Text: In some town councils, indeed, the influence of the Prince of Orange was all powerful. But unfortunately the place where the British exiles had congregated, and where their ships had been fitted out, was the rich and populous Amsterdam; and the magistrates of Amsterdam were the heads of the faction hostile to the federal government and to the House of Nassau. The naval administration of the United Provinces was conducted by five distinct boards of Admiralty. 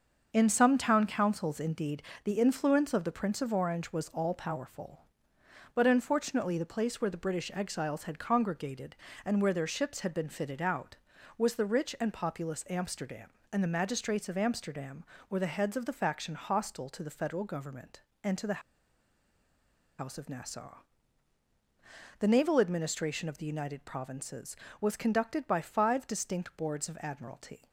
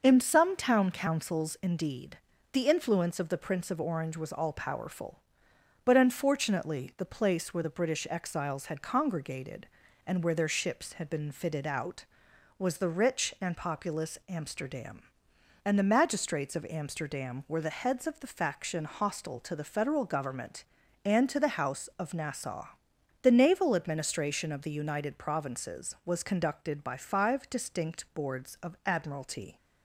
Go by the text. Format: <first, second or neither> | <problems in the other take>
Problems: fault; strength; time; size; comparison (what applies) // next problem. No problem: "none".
second | starts louder than the rest; until 1.3 s; 6.5 dB // pauses between "the" and "House"; strong; at 18.6 s; 1.3 s long